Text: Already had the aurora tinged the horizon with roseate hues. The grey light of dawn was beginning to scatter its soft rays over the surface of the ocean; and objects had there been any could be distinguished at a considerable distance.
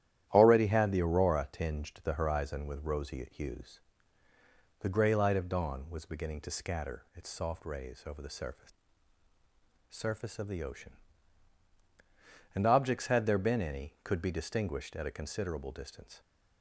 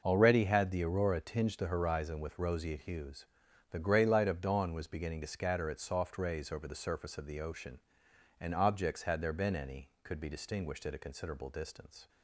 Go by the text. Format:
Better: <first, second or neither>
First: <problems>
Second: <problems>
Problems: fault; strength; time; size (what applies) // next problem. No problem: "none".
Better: second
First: starts louder than the rest; strong; until 1.3 s; 11.5 dB // says "surface" twice; at 9.8 s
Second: none